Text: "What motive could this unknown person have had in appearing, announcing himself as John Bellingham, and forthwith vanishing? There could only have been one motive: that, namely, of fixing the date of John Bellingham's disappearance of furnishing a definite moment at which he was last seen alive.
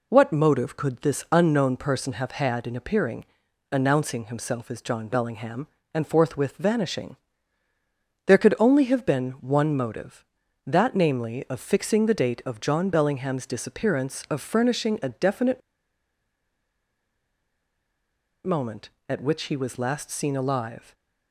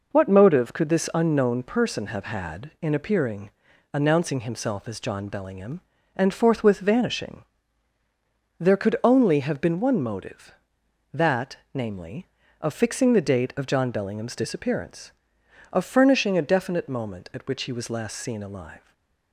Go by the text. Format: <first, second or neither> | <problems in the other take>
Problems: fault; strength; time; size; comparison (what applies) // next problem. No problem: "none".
second | pauses between "definite" and "moment"; strong; at 15.6 s; 2.8 s long // stays silent after the last word; slight; from 20.7 s on; 0.6 s long; slight in the second